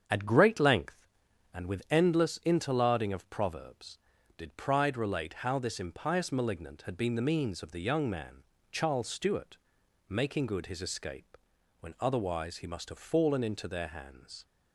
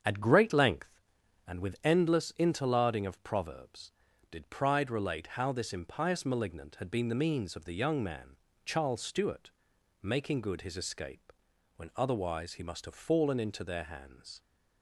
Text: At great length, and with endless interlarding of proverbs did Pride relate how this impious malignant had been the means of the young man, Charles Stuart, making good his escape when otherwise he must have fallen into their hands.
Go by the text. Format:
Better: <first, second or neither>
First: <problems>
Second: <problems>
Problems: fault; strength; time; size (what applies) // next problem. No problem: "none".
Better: neither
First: starts louder than the rest; strong; until 1.0 s; 7.5 dB // pauses between "escape" and "when"; at 11.3 s; 0.41 s long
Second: starts louder than the rest; strong; until 1.4 s; 7.5 dB // pauses between "escape" and "when"; at 11.3 s; 0.42 s long